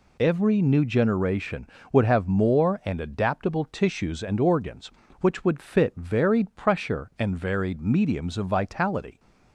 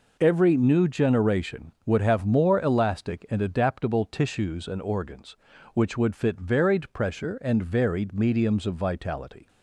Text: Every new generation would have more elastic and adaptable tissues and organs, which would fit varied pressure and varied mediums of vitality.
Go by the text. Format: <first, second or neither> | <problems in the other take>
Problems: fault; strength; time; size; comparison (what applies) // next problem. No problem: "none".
second | skips "elastic"; at 2.8 s